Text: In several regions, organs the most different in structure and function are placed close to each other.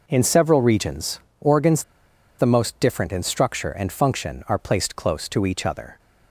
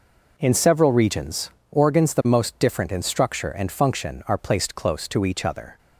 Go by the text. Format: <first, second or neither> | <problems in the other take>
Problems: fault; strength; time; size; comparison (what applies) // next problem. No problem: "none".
second | pauses between "organs" and "the"; noticeable; at 1.8 s; 0.54 s long